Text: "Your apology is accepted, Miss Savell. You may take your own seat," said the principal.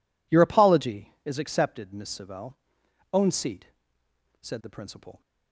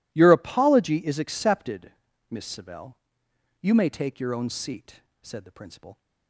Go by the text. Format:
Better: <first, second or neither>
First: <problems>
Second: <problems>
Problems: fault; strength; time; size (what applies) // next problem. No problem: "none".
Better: second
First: skips "You may take your"; at 2.8 s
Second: none